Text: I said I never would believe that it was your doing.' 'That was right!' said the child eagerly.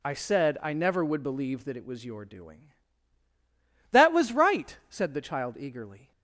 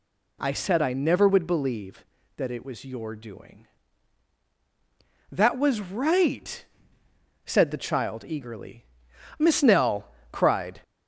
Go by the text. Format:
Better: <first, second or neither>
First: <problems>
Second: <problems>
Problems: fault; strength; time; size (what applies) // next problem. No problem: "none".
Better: first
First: none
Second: goes on to say "Miss Nell cried"; from 9.3 s on; 1.4 s long